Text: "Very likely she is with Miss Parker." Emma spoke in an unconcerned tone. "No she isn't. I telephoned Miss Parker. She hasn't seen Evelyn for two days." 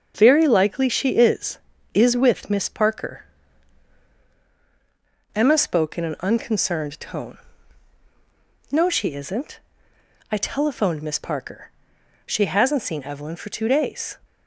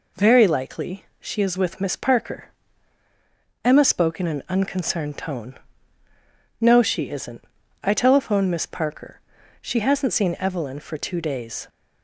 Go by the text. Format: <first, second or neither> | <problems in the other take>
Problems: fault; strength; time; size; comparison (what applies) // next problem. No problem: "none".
second | starts louder than the rest; until 1.1 s; 6.5 dB // says "is" twice; at 1.9 s